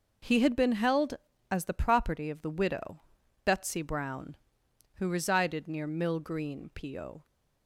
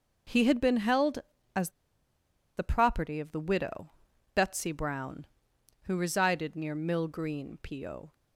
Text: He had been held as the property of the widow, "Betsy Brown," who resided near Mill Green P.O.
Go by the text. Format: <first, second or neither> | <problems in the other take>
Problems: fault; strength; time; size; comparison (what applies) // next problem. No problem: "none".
first | pauses between "as" and "the"; noticeable; at 1.6 s; 0.87 s long